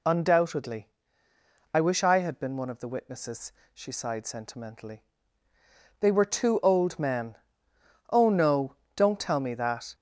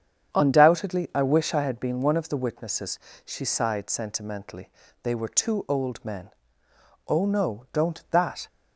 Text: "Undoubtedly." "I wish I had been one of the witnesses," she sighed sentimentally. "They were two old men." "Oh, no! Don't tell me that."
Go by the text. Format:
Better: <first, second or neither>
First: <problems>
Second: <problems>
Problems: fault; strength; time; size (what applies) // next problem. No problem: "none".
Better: first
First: none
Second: starts louder than the rest; strong; until 1.3 s; 8 dB // skips "tell me"; at 8.0 s